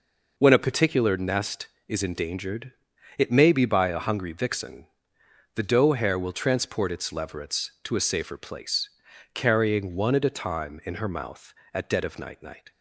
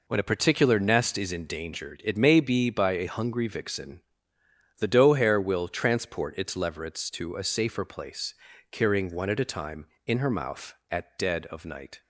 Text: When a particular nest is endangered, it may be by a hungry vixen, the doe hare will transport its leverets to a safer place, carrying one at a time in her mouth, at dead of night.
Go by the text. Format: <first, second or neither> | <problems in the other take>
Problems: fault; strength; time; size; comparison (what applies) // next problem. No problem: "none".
second | says "night" twice; at 12.4 s